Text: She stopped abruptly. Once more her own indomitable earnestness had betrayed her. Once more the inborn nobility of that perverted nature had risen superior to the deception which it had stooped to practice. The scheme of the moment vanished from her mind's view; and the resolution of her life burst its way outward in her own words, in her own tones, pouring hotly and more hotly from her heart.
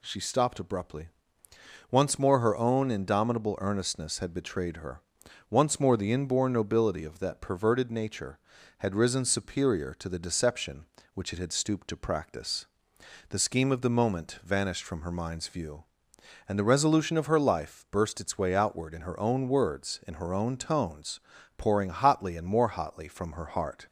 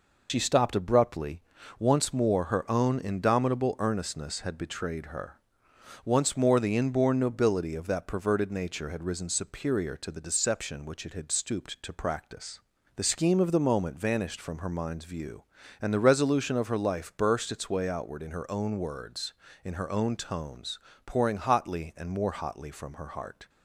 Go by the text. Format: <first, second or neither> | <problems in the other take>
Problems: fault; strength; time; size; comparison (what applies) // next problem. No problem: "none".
first | loses the start of "She"; at 0.2 s; 70 ms